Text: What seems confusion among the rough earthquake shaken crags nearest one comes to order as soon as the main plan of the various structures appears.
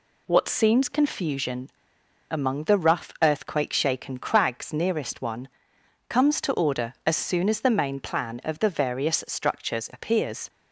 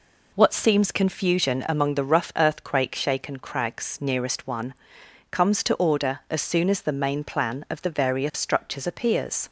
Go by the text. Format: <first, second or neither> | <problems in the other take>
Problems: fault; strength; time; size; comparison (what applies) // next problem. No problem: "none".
second | pauses between "confusion" and "among"; noticeable; at 1.6 s; 0.61 s long // pauses between "one" and "comes"; noticeable; at 5.4 s; 0.58 s long; noticeable in the second